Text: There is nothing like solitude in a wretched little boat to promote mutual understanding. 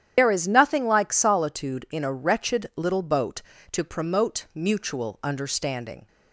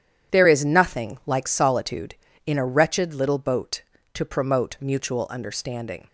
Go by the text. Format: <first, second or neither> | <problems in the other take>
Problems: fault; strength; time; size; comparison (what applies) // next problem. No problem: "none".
second | loses the start of "There"; at 0.1 s; 80 ms // starts louder than the rest; strong; until 1.1 s; 10 dB